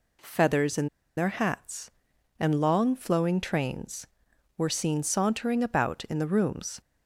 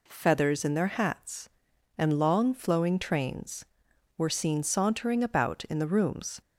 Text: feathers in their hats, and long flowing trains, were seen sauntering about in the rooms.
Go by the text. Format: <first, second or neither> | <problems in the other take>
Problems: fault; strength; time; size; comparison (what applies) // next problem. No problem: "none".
second | pauses between "in" and "their"; slight; at 0.8 s; 0.29 s long